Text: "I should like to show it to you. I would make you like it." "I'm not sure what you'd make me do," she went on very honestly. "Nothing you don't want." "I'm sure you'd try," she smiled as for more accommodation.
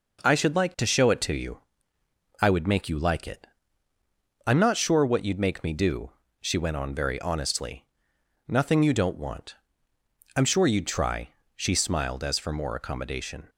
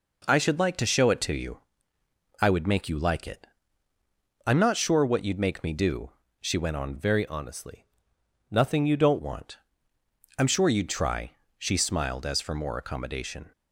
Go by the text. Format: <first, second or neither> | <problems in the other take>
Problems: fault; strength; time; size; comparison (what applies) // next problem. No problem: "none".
first | changes voice from "very" to "don't"; from 6.9 to 9.1 s; 2.2 s long